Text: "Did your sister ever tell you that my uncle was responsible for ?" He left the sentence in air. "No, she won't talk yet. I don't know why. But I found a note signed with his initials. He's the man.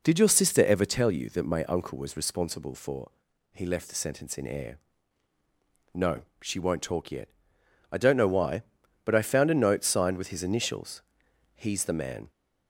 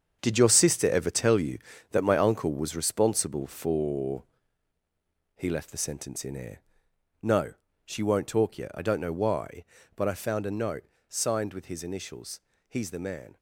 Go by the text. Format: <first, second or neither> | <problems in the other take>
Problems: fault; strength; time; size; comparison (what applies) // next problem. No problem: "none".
first | gets quieter; strong; throughout; 7 dB // pauses between "note" and "signed"; slight; at 10.8 s; 0.24 s long